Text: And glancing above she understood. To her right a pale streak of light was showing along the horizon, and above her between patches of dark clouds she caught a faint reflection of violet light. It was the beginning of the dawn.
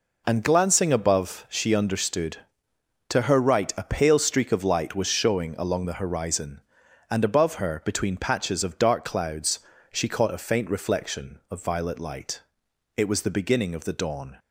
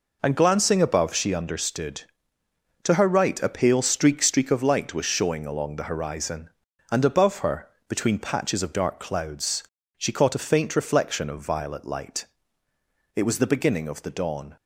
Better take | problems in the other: first | says "streak" twice; at 4.2 s // pauses between "her" and "between"; slight; at 7.6 s; 0.20 s long // pauses between "clouds" and "she"; slight; at 9.6 s; 0.36 s long; slight in the first

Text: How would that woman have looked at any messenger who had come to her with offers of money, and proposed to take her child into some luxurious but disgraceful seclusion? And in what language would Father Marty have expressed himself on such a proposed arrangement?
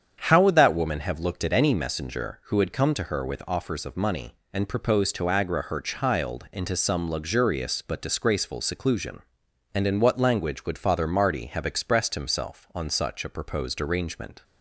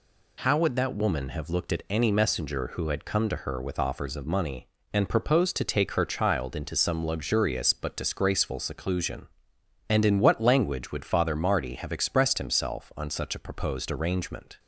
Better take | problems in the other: second | starts louder than the rest; strong; until 1.2 s; 8 dB // says "agra" for "take"; at 5.2 s

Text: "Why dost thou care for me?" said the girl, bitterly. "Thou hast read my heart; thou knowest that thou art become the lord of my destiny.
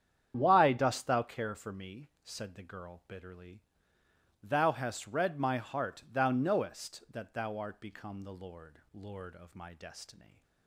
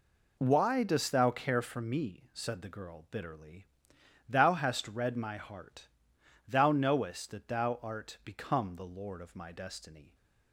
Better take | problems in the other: second | starts louder than the rest; strong; until 1.3 s; 8.5 dB // says "lord" twice; at 8.9 s

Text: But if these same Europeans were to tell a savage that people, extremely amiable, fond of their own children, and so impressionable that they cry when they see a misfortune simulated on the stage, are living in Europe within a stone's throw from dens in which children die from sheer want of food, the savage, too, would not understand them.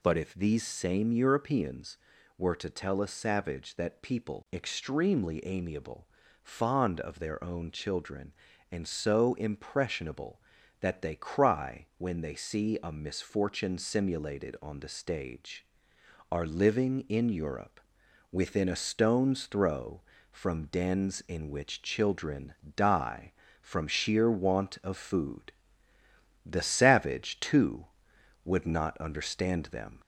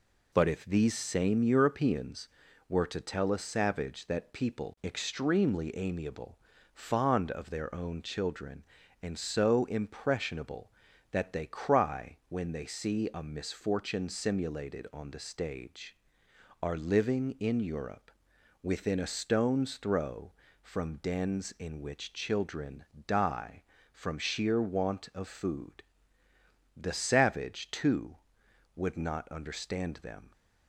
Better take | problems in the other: second | gets louder; slight; throughout; 2 dB // pauses between "Europe" and "within"; noticeable; at 17.7 s; 0.54 s long; noticeable in the second // pauses between "children" and "die"; slight; at 22.5 s; 0.20 s long; slight in the second

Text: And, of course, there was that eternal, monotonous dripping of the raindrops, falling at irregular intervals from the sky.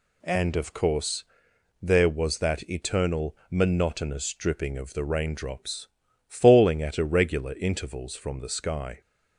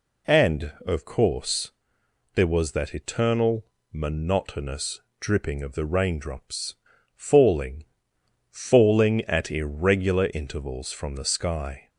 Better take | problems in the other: first | pauses between "monotonous" and "dripping"; slight; at 5.0 s; 0.18 s long // says "falling" twice; at 8.5 s

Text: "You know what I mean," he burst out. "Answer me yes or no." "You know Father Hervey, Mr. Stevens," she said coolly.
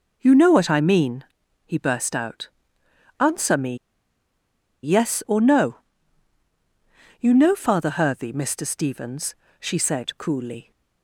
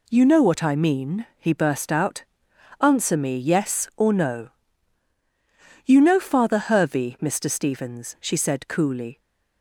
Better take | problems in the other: second | pauses between "me" and "yes"; at 3.7 s; 1.0 s long

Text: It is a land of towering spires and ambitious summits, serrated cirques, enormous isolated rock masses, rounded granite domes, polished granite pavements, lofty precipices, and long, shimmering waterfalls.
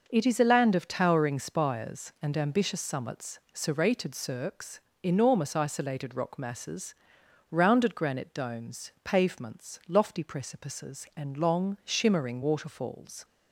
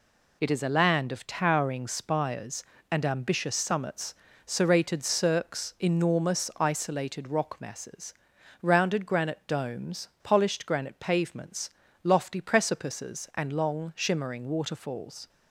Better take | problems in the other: second | skips "polished granite"; at 8.9 s

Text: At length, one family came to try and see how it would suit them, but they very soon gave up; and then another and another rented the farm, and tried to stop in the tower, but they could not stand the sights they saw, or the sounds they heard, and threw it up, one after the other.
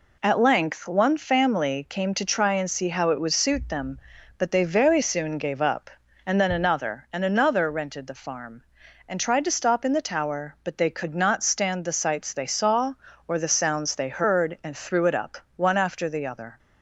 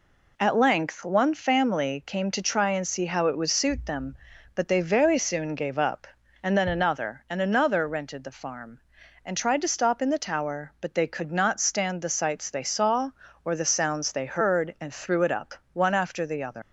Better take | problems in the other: first | leaves "other" unfinished; at 16.6 s; 130 ms

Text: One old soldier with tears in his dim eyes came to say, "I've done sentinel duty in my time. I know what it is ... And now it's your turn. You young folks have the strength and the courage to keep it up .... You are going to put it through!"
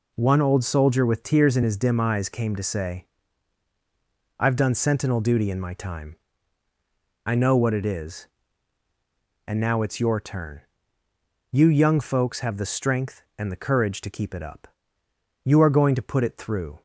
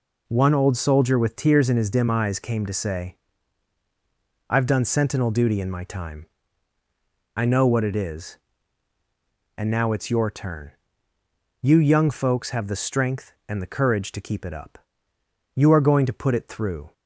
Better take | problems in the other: neither | none

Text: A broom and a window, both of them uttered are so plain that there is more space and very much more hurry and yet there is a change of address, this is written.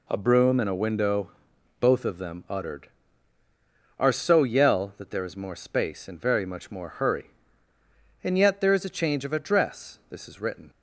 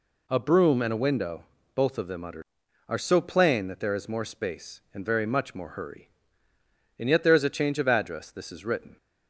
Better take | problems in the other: second | says "yell" for "plain"; at 4.4 s

